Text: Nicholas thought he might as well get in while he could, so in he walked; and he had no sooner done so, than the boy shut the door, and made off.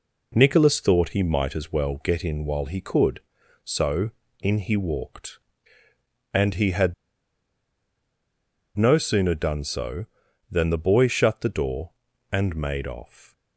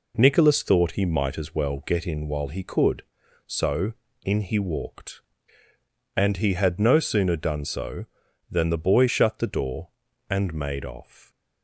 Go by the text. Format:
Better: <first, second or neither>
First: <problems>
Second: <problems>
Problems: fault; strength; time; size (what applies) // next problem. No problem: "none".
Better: second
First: pauses between "had" and "no"; strong; at 6.9 s; 1.8 s long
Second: none